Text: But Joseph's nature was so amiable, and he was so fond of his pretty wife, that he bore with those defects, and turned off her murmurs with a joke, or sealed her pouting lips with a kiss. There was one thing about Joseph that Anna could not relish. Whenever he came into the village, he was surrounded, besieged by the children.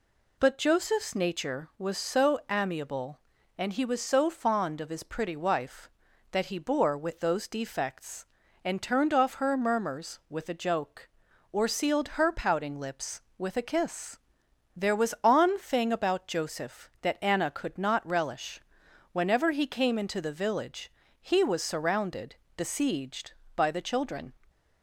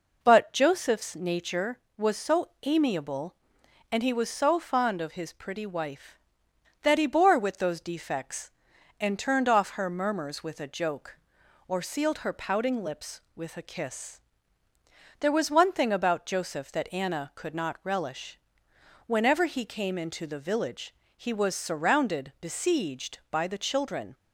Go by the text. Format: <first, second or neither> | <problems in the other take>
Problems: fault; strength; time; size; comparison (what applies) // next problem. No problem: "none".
second | says "on" for "one"; at 15.2 s